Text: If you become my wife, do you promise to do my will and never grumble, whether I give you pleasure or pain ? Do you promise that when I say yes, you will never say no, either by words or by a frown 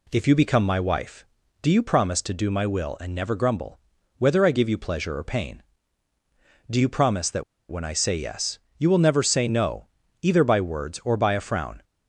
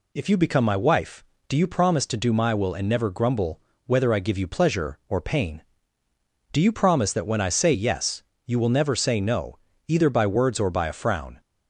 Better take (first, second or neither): second